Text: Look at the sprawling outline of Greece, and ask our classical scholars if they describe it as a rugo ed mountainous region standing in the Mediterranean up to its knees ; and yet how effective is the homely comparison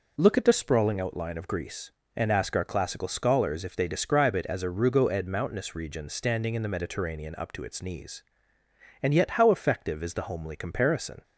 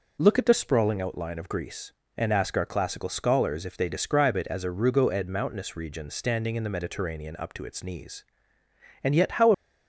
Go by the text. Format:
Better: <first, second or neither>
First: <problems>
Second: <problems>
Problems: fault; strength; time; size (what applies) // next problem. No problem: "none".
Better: first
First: none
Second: stops before "effective is the homely comparison"; at 9.5 s